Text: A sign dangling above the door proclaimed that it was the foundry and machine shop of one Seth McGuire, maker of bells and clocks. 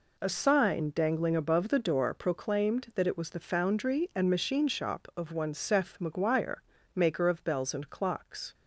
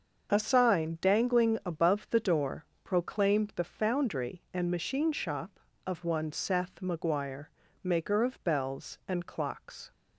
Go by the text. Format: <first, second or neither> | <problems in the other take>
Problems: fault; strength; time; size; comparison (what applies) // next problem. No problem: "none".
first | starts louder than the rest; until 1.3 s; 6.5 dB // pauses between "door" and "proclaimed"; slight; at 2.6 s; 0.20 s long // skips "that it was"; at 3.5 s